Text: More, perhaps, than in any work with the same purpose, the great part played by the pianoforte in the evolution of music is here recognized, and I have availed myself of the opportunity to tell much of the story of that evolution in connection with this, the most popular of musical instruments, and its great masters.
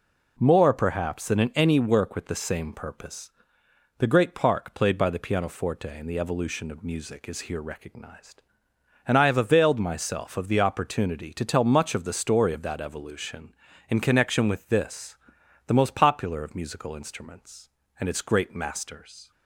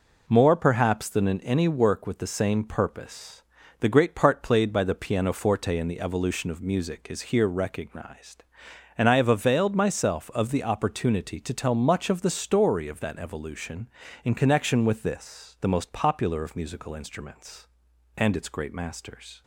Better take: second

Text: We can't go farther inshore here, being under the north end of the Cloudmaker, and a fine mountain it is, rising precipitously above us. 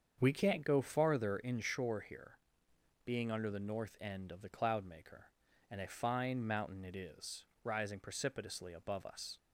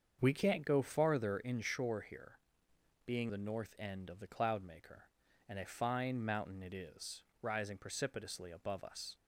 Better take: first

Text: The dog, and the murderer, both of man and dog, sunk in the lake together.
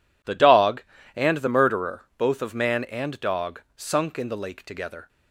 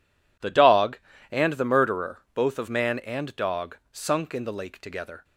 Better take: neither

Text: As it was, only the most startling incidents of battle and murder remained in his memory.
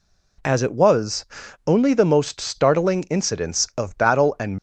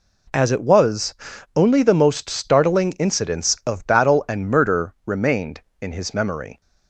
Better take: second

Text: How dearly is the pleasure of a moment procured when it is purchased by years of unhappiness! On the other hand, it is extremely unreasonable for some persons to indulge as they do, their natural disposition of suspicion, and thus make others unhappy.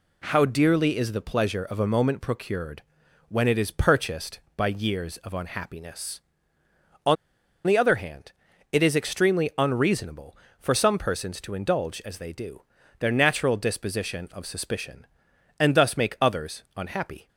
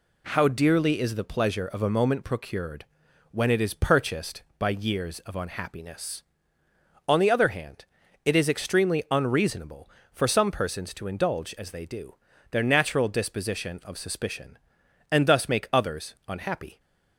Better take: second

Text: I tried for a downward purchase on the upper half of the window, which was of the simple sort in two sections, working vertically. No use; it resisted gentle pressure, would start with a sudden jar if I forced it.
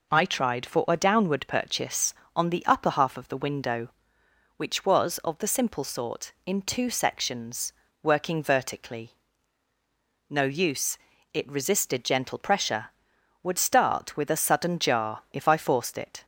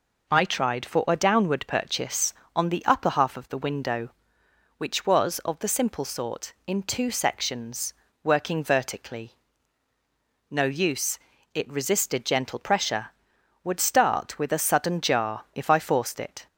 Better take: neither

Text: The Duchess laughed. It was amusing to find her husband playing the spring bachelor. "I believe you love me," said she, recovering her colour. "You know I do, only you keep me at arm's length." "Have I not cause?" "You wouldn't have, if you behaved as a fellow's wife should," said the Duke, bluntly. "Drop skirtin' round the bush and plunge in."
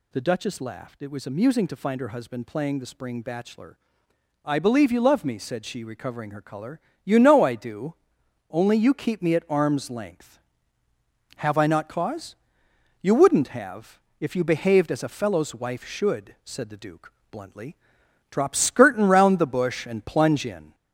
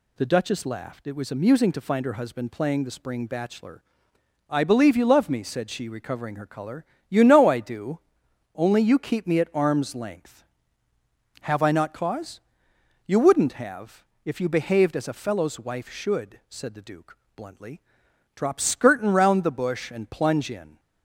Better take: second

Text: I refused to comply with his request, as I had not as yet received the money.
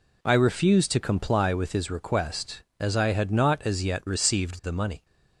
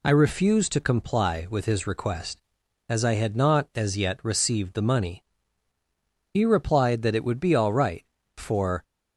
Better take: first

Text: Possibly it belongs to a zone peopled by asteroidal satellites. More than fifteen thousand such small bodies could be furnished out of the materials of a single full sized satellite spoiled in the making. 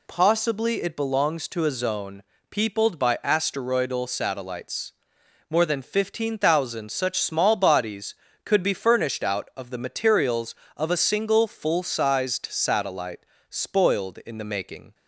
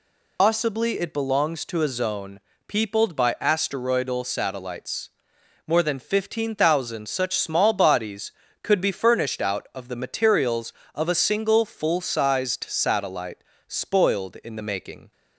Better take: first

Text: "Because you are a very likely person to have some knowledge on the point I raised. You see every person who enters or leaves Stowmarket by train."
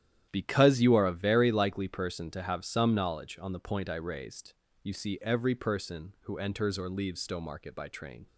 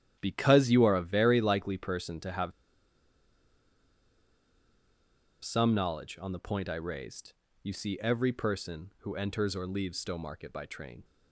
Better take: first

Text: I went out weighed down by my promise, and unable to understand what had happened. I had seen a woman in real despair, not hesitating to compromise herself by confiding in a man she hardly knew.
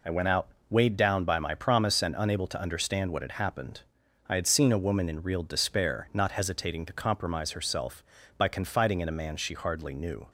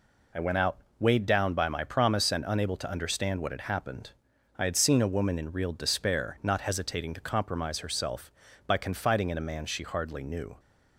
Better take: neither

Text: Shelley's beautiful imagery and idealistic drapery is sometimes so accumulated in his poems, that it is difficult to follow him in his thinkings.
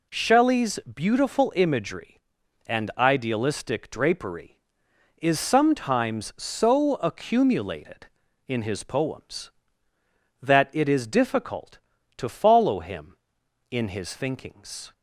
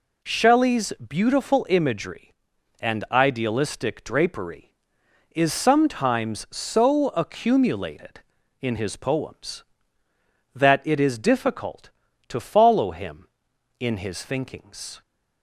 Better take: neither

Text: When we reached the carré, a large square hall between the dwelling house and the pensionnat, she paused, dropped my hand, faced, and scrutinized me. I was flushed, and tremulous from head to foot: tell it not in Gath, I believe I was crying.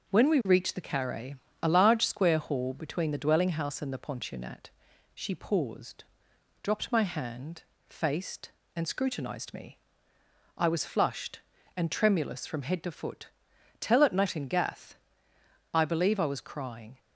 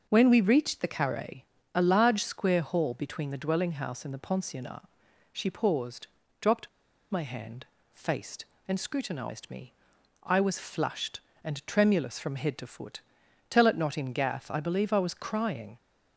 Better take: first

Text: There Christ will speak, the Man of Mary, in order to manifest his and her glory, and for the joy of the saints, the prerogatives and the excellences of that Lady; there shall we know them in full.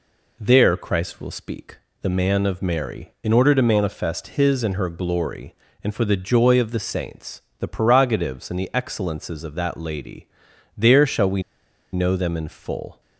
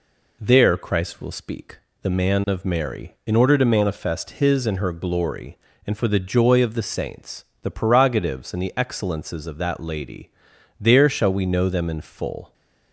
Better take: second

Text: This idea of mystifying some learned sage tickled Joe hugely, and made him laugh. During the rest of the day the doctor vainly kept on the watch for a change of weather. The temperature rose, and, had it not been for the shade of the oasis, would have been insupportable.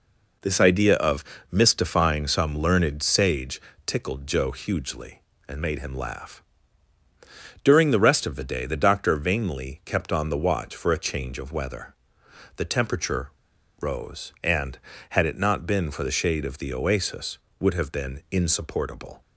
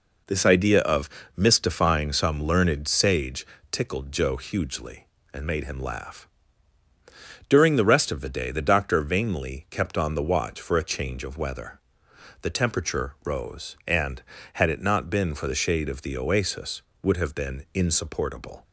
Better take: second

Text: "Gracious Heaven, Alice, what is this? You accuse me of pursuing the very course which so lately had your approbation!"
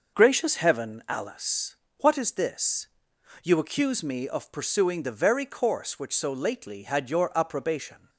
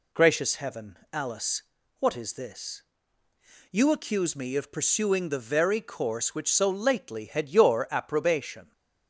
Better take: neither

